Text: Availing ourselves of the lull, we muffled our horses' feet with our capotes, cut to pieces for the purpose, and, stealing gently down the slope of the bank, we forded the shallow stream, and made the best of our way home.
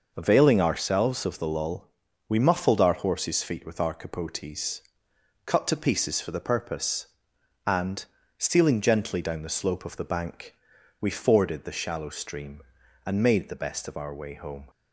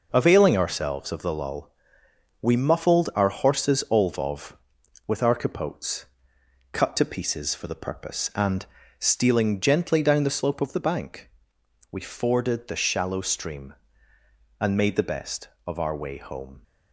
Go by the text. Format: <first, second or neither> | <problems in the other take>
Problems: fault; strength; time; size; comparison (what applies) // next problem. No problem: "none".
first | says "olvov" for "feet"; at 3.9 s